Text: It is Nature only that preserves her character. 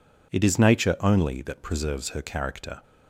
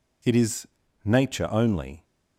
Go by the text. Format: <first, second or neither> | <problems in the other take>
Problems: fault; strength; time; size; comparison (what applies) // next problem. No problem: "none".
first | pauses between "is" and "Nature"; at 0.6 s; 0.38 s long // stops before "that preserves her character"; at 2.0 s